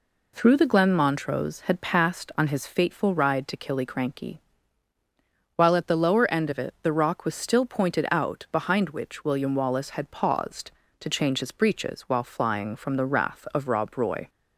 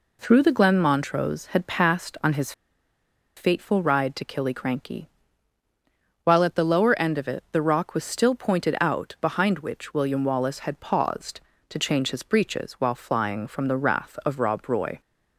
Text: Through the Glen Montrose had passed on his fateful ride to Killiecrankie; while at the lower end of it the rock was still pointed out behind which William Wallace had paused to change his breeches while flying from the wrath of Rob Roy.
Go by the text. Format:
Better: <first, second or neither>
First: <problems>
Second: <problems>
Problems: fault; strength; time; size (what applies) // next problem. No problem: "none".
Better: first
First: none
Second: pauses between "his" and "fateful"; noticeable; at 2.5 s; 0.84 s long